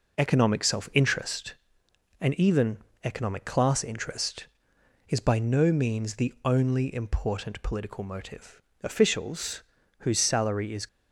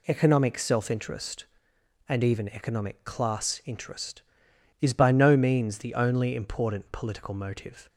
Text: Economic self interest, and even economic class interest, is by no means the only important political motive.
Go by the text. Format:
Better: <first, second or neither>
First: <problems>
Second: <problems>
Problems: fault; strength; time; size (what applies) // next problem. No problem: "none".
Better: second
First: pauses between "even" and "economic"; slight; at 2.7 s; 0.26 s long // goes on to say "Officials whose salary is"; strong; from 8.8 s on; 2.0 s long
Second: none